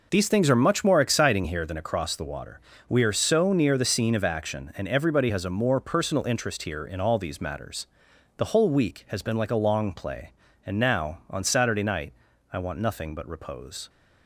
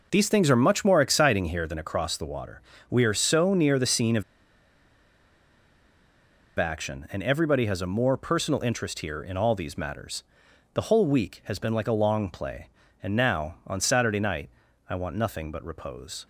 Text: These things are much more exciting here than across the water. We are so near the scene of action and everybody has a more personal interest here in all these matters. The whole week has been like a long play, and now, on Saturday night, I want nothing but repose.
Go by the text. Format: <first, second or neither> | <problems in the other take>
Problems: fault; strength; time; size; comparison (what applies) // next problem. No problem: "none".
first | pauses between "of" and "action"; strong; at 4.2 s; 2.3 s long